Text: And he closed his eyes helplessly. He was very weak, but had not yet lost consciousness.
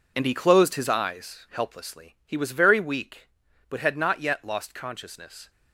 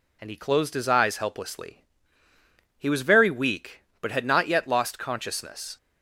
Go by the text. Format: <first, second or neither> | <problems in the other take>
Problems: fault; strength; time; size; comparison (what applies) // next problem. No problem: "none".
second | gets quieter; strong; throughout; 10.5 dB